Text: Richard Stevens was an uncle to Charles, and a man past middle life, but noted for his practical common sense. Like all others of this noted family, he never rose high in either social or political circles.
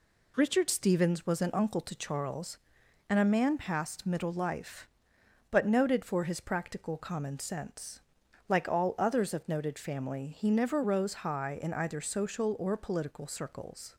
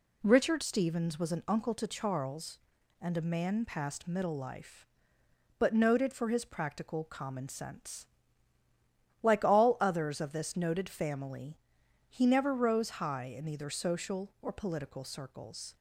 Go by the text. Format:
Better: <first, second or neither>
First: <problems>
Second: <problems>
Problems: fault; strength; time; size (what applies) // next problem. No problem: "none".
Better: second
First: skips "this"; at 9.4 s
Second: none